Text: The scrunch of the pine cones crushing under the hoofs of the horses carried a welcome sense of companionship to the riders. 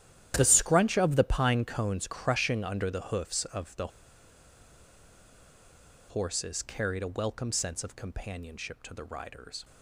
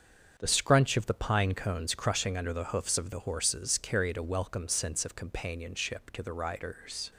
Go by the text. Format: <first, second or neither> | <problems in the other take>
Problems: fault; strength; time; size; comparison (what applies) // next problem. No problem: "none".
second | starts louder than the rest; strong; until 1.3 s; 11.5 dB; also in the second // pauses between "the" and "horses"; strong; at 3.8 s; 2.2 s long